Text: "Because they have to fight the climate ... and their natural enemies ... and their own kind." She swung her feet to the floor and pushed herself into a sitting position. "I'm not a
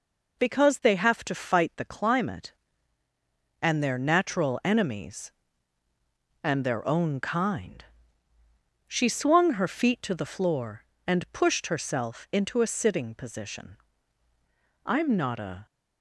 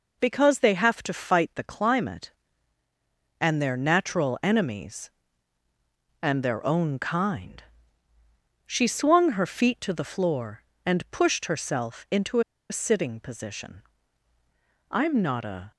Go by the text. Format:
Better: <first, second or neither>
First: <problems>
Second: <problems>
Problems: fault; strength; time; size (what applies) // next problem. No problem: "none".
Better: first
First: none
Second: pauses between "into" and "a"; slight; at 12.3 s; 0.29 s long